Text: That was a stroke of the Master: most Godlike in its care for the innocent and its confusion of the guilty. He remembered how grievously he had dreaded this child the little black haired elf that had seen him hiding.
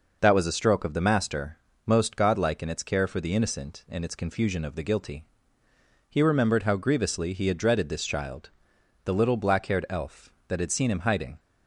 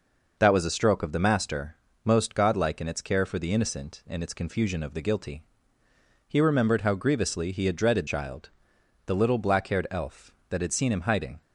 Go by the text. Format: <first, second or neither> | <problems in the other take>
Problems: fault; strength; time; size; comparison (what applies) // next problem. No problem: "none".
first | skips "this"; at 8.0 s // pauses between "child" and "the"; noticeable; at 8.4 s; 0.58 s long; noticeable in the first